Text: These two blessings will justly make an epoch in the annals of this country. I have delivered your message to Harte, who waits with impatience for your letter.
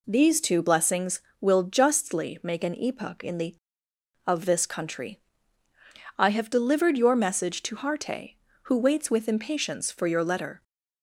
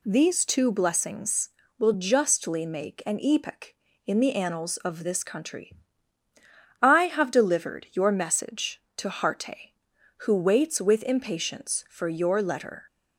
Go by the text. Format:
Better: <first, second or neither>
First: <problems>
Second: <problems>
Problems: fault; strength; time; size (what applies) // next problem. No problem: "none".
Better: second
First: skips "annals"; at 3.9 s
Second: none